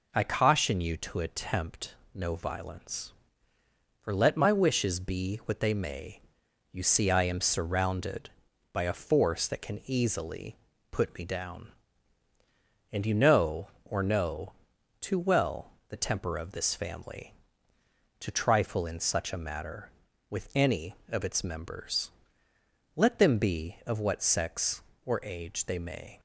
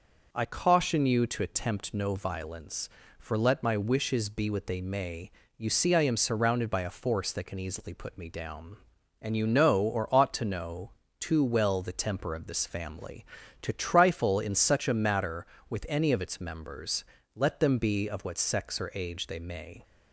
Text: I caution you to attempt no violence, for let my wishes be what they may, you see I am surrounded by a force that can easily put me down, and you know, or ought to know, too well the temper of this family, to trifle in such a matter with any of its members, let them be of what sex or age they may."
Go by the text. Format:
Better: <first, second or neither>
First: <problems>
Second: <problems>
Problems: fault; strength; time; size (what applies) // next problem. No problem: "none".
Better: second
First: pauses between "attempt" and "no"; slight; at 1.9 s; 0.22 s long // pauses between "easily" and "put"; slight; at 10.5 s; 0.34 s long // skips "ought to"; at 14.0 s // pauses between "well" and "the"; slight; at 15.6 s; 0.20 s long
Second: none